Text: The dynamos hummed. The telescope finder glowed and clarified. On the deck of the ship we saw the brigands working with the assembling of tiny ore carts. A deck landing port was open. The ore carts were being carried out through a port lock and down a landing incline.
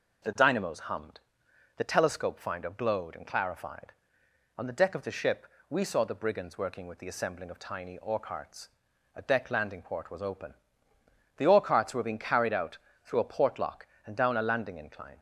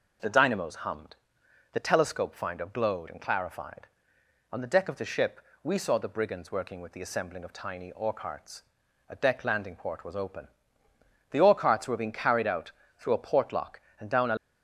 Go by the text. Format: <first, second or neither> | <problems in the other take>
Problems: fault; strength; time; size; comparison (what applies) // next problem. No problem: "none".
first | pauses between "ship" and "we"; slight; at 5.3 s; 0.24 s long; slight in the first // pauses between "out" and "through"; slight; at 12.7 s; 0.26 s long; slight in the first // stops before "landing incline"; at 14.3 s